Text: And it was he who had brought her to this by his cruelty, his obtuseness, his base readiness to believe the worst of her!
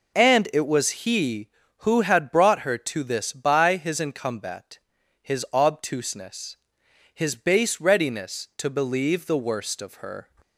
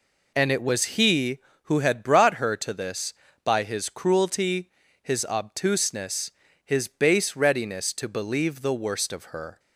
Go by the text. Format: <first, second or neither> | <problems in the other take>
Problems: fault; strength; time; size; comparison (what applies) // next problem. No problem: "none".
second | says "incumbat" for "cruelty"; at 3.9 s